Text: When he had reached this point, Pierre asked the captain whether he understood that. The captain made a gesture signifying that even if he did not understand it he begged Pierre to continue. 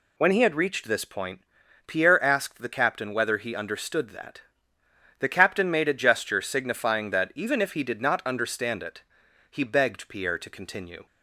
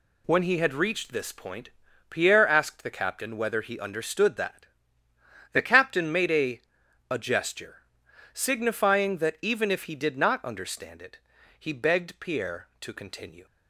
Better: first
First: pauses between "it" and "he"; noticeable; at 9.0 s; 0.48 s long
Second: says "a" twice; at 7.0 s // pauses between "gesture" and "signifying"; noticeable; at 7.8 s; 0.52 s long // pauses between "it" and "he"; at 11.1 s; 0.40 s long

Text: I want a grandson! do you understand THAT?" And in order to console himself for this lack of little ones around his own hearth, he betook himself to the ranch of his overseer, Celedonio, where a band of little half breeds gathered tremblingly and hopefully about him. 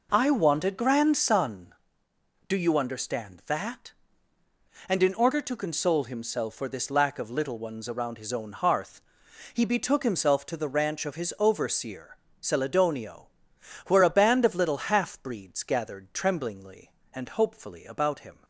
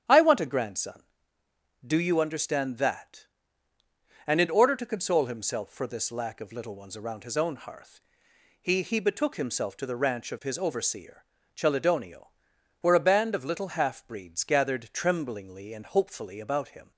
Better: first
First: none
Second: starts louder than the rest; strong; until 1.9 s; 9.5 dB // says "he" twice; at 8.8 s

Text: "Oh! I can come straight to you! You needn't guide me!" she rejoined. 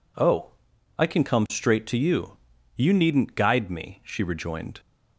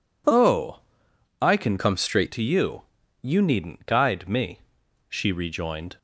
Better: first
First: none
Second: changes voice from "come" to "straight"; from 1.7 to 2.3 s; 0.6 s long

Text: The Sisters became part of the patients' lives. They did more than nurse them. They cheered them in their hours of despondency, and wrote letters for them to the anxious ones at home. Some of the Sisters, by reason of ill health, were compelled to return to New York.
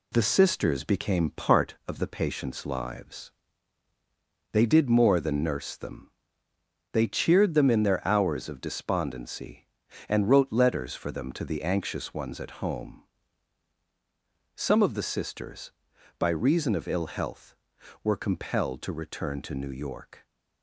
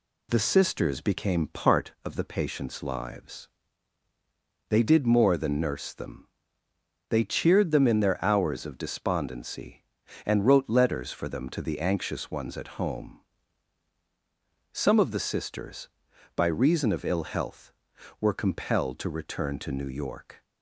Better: second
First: gets quieter; noticeable; throughout; 5 dB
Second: none

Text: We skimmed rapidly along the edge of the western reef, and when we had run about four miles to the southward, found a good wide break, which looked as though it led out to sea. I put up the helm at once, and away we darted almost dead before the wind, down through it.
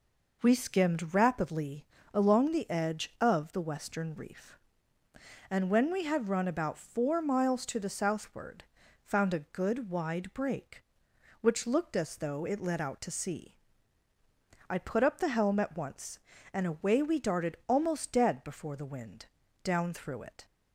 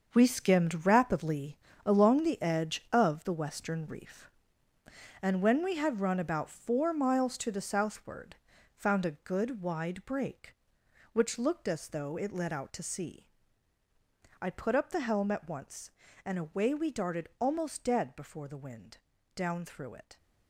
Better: first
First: pauses between "rapidly" and "along"; slight; at 1.8 s; 0.28 s long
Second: gets quieter; strong; throughout; 10 dB // pauses between "rapidly" and "along"; slight; at 1.5 s; 0.28 s long

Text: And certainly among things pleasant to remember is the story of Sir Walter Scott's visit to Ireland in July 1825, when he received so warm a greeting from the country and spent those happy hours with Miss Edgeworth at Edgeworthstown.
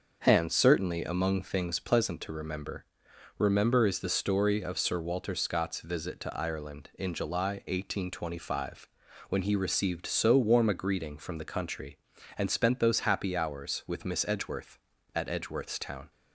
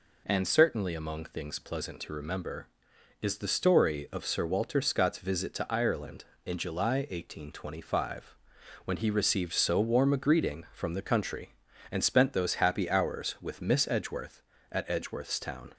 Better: second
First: starts louder than the rest; until 1.2 s; 6.5 dB // says "remember" twice; at 3.3 s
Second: none

